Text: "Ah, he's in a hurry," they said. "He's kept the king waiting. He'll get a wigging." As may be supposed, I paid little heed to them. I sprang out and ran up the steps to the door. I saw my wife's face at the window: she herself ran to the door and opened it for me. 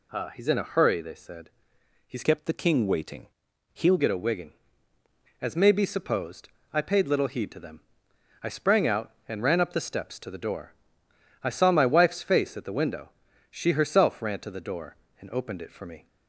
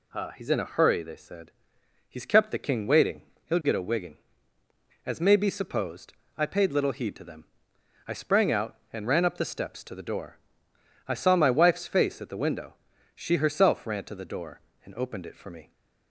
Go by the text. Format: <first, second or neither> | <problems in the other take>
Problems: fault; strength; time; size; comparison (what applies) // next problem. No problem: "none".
second | changes voice from "kept" to "He'll"; from 2.2 to 3.9 s; 1.7 s long